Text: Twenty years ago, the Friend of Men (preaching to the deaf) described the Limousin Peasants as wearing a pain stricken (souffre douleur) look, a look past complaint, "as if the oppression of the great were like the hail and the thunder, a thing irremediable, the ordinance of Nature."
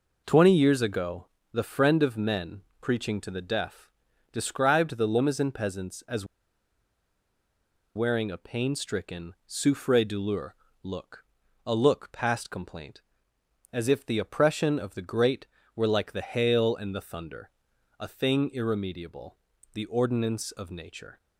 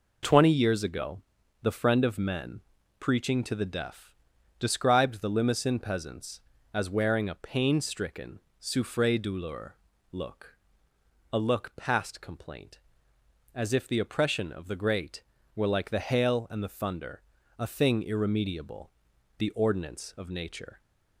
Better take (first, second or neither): second